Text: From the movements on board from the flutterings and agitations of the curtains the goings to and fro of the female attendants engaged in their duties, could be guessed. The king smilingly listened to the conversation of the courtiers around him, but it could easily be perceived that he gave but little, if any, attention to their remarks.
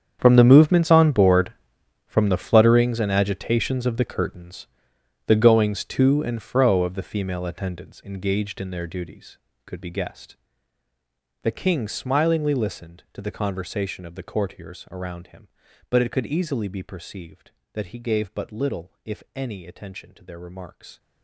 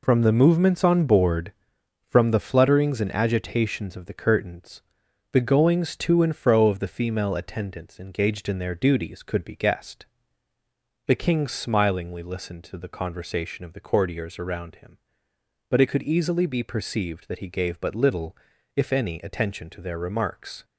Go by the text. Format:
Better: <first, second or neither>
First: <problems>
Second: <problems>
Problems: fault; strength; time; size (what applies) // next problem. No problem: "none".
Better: second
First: gets quieter; strong; throughout; 16.5 dB // pauses between "curtains" and "the"; noticeable; at 4.6 s; 0.60 s long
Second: pauses between "curtains" and "the"; noticeable; at 4.8 s; 0.50 s long